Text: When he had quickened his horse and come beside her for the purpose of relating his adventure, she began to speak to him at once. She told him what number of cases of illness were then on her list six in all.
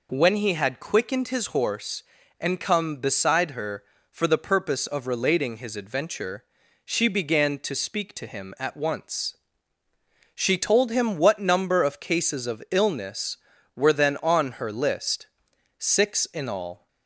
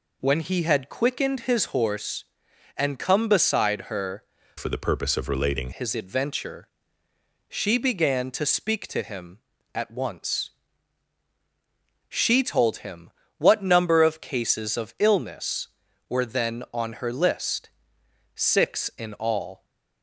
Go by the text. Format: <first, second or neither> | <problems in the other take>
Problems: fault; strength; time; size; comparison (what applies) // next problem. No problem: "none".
first | changes voice from "for" to "relating"; from 4.5 to 5.7 s; 1.2 s long // pauses between "him" and "what"; slight; at 13.1 s; 0.28 s long // pauses between "list" and "six"; noticeable; at 17.7 s; 0.66 s long; noticeable in the first